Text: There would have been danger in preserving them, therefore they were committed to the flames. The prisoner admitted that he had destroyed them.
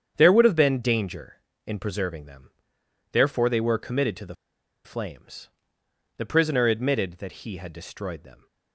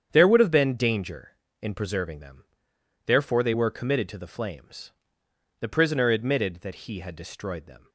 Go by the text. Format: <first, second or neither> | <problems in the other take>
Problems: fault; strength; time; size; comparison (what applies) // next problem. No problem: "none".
second | starts louder than the rest; strong; until 1.1 s; 8.5 dB; strong in the second // pauses between "the" and "flames"; noticeable; at 4.3 s; 0.50 s long